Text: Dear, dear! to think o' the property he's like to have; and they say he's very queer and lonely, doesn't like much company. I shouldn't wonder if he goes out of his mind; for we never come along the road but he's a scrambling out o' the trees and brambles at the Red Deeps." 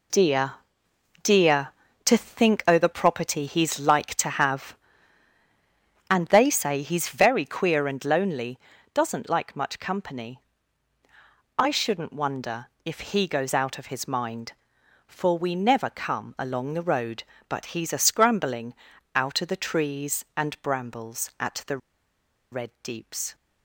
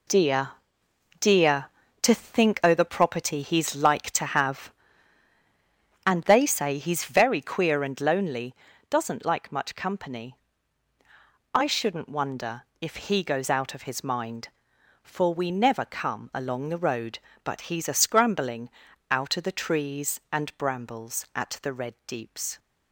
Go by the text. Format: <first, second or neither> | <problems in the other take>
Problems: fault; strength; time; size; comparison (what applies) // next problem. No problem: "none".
second | pauses between "wonder" and "if"; slight; at 12.6 s; 0.16 s long; slight in the second // pauses between "scrambling" and "out"; at 18.7 s; 0.42 s long; also in the second // pauses between "the" and "Red"; noticeable; at 21.7 s; 0.74 s long